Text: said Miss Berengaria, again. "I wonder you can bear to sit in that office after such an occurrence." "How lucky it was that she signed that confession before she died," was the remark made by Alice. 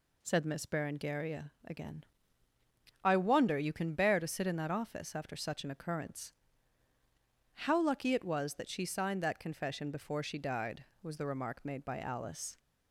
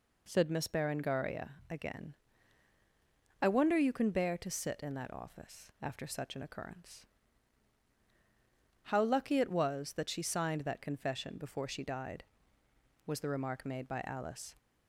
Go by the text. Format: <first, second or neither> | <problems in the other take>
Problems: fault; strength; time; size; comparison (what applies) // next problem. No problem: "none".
neither | none